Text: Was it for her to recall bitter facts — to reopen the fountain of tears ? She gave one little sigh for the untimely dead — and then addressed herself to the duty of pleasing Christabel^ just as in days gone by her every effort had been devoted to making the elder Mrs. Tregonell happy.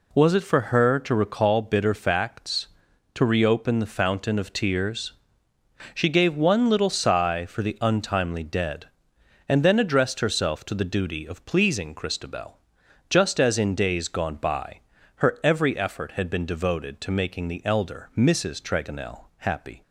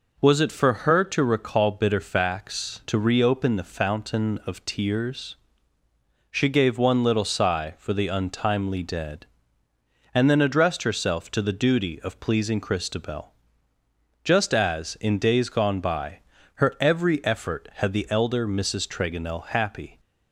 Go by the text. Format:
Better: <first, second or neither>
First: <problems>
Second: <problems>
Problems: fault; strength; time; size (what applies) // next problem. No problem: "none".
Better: first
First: pauses between "Christabel" and "just"; noticeable; at 12.5 s; 0.52 s long // pauses between "by" and "her"; slight; at 14.7 s; 0.36 s long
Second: pauses between "Christabel" and "just"; noticeable; at 13.3 s; 0.92 s long // pauses between "by" and "her"; slight; at 16.1 s; 0.36 s long // skips "been devoted to making"; at 17.9 s